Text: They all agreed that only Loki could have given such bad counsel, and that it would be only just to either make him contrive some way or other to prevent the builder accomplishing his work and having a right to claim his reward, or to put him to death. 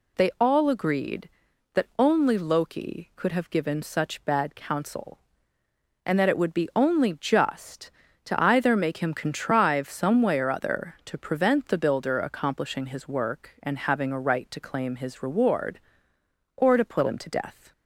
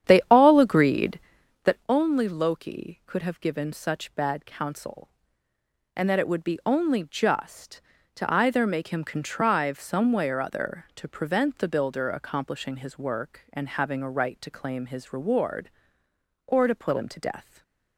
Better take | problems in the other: first | starts louder than the rest; strong; until 1.9 s; 9.5 dB // stays silent after the last word; slight; from 17.4 s on; 0.5 s long

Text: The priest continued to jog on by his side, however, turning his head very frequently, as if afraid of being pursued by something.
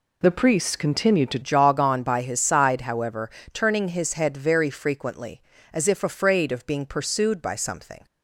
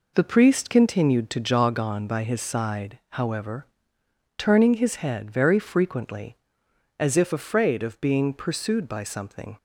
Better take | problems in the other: second | changes voice at "jog"; from 1.4 s on; 6.6 s long

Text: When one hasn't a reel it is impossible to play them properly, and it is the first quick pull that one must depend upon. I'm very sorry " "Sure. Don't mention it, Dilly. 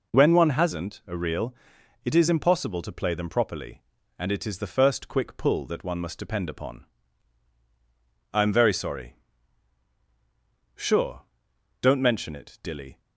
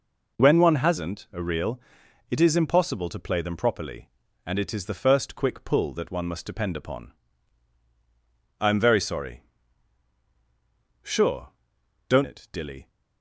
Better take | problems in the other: first | pauses between "reel" and "it"; noticeable; at 1.7 s; 0.52 s long; noticeable in the first // skips "mention"; at 12.2 s

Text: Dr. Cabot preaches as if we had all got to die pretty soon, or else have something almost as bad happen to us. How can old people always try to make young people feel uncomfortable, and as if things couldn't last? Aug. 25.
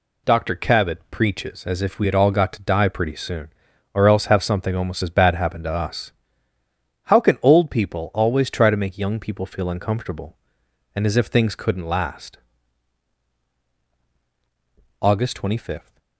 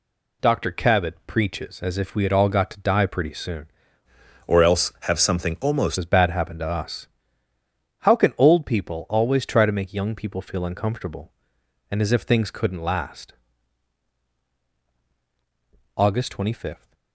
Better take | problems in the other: first | changes voice from "or" to "almost"; from 4.4 to 5.9 s; 1.5 s long

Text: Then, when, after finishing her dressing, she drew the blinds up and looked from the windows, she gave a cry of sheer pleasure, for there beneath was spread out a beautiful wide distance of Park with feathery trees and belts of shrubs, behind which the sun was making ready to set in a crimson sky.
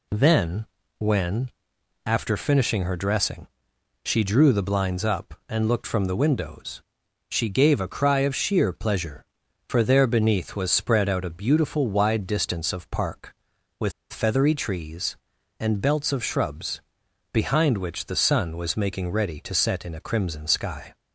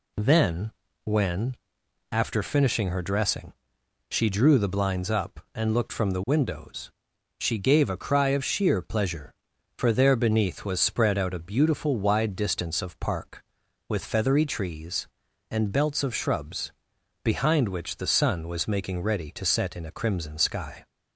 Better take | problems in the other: second | pauses between "with" and "feathery"; slight; at 13.9 s; 0.20 s long

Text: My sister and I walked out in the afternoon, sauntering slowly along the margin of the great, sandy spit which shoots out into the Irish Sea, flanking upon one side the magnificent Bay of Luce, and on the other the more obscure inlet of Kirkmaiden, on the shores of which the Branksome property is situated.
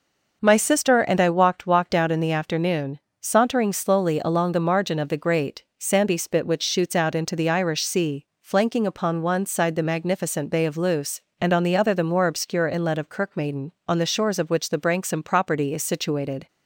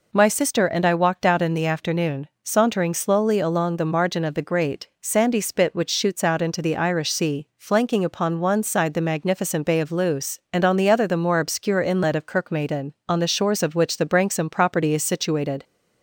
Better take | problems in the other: second | says "walked" twice; at 1.6 s

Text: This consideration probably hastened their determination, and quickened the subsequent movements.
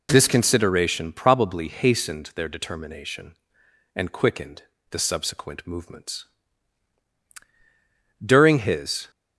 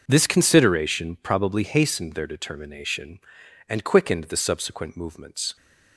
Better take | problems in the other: second | pauses between "quickened" and "the"; slight; at 4.6 s; 0.26 s long // goes on to say "During his"; noticeable; from 8.2 s on; 0.90 s long

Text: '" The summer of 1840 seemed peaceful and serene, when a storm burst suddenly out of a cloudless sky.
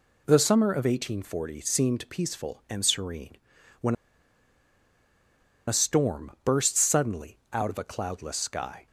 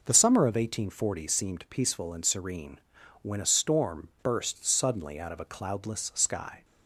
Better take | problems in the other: second | pauses between "when" and "a"; strong; at 3.9 s; 1.7 s long

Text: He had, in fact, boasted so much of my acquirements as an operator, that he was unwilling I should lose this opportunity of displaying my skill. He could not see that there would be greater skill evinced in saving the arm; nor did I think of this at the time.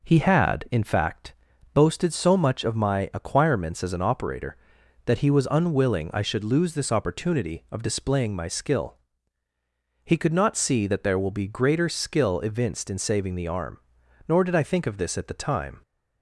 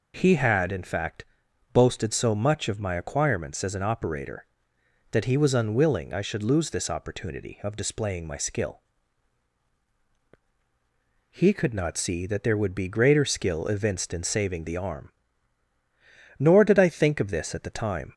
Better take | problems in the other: second | says "will" for "would"; at 11.1 s

